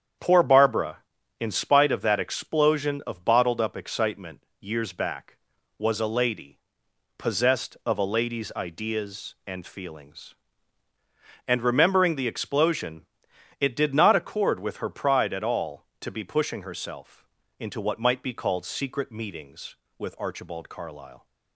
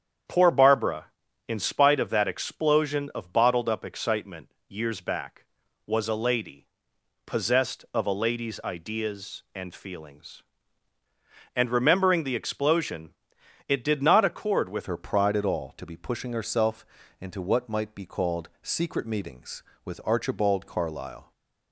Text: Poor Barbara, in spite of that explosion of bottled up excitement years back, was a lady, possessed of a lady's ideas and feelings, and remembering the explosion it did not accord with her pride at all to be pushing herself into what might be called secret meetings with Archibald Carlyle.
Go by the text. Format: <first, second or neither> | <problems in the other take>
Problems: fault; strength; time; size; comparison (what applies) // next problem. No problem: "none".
first | starts louder than the rest; strong; until 1.7 s; 8.5 dB; strong in the first // pauses between "excitement" and "years"; slight; at 4.4 s; 0.18 s long; slight in the first // pauses between "explosion" and "it"; noticeable; at 13.1 s; 0.58 s long; noticeable in the first // changes voice at "her"; from 14.8 s on; 6.5 s long // pauses between "herself" and "into"; slight; at 16.8 s; 0.36 s long; slight in the first